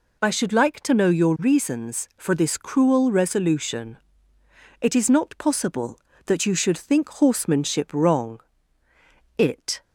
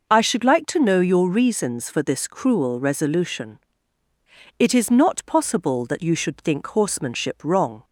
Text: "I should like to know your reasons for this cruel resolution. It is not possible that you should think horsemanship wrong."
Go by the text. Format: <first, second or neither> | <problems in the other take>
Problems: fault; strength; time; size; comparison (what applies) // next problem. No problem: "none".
second | goes on to say "It"; slight; from 9.3 s on; 0.44 s long